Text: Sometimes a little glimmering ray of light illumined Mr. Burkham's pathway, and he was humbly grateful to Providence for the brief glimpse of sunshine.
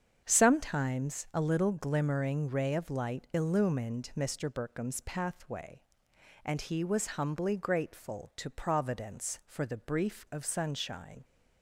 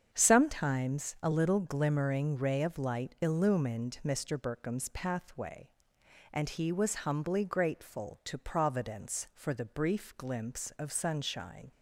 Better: second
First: starts louder than the rest; strong; until 1.2 s; 7.5 dB // skips "glimpse"; at 10.2 s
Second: starts louder than the rest; strong; until 1.1 s; 7.5 dB

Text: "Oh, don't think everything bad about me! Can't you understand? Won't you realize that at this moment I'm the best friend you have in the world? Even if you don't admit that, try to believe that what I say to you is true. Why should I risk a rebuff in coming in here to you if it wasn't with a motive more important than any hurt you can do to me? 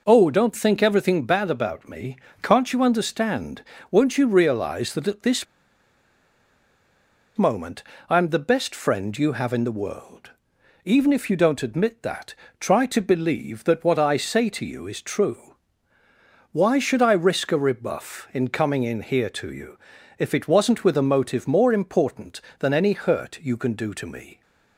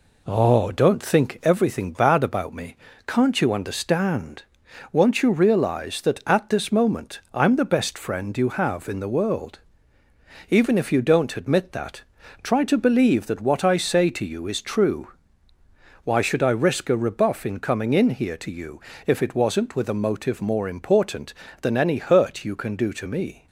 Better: second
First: pauses between "this" and "moment"; strong; at 5.4 s; 1.9 s long // pauses between "moment" and "I'm"; slight; at 7.8 s; 0.26 s long // pauses between "you" and "if"; at 19.7 s; 0.40 s long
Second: pauses between "you" and "if"; slight; at 18.8 s; 0.26 s long

